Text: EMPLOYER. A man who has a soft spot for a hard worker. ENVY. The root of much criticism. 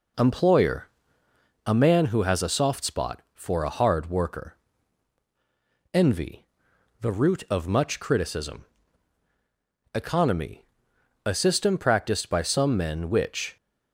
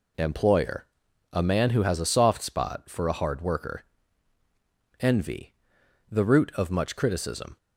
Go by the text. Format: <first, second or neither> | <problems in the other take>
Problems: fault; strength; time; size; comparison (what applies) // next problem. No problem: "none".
second | goes on to say "ECONOMY A system practiced by some men which"; strong; from 9.9 s on; 3.6 s long